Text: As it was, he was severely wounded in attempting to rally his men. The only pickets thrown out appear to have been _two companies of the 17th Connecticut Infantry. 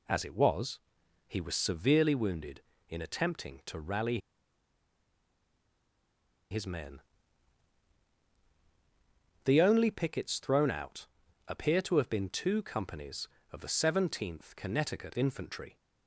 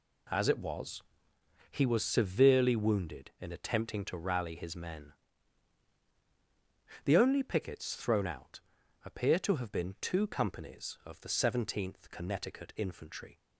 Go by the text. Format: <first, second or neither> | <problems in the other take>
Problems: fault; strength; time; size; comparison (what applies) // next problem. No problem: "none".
second | pauses between "rally" and "his"; strong; at 4.1 s; 2.3 s long // pauses between "out" and "appear"; at 11.0 s; 0.42 s long; also in the second